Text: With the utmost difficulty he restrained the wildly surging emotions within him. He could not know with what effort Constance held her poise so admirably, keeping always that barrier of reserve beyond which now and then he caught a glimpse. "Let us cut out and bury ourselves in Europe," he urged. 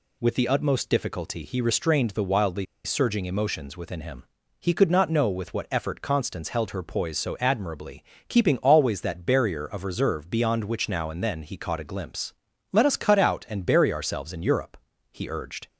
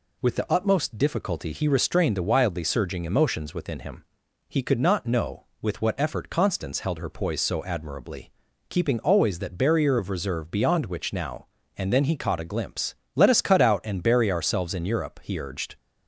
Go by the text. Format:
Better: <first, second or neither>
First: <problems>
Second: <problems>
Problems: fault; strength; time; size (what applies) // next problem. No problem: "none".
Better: second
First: pauses between "wildly" and "surging"; slight; at 2.6 s; 0.20 s long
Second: none